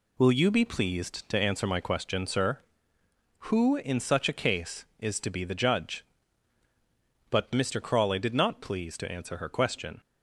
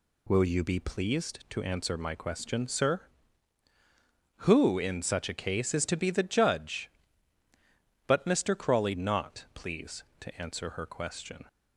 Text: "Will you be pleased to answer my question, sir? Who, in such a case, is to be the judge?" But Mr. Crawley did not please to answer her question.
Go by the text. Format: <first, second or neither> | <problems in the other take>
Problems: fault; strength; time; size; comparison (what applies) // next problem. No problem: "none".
first | skips "did"; at 8.9 s